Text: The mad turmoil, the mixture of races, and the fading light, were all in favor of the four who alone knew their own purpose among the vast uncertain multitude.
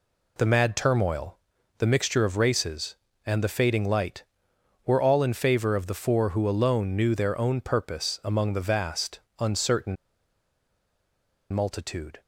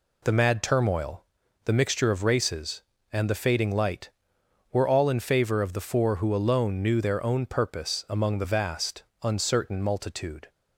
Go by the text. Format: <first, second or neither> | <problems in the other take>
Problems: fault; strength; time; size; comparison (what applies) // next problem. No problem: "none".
second | pauses between "vast" and "uncertain"; slight; at 9.1 s; 0.20 s long; slight in the second // pauses between "uncertain" and "multitude"; strong; at 9.9 s; 1.5 s long